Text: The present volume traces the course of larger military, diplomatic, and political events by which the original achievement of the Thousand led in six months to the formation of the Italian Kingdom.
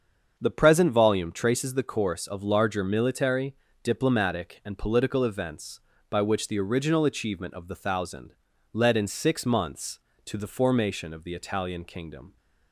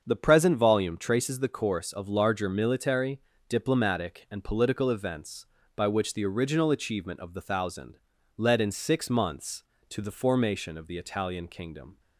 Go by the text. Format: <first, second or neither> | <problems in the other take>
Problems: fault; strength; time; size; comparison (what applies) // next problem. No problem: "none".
neither | starts louder than the rest; the same in both // pauses between "Thousand" and "led"; the same in both